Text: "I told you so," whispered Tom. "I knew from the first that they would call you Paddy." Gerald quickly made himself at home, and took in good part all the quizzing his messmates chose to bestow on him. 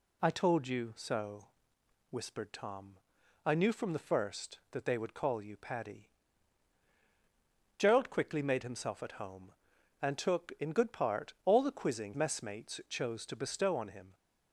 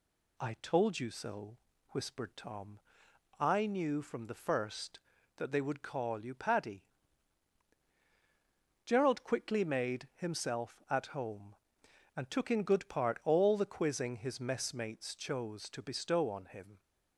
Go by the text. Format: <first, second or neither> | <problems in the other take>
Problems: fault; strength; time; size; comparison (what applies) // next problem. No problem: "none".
second | skips "his"; at 12.1 s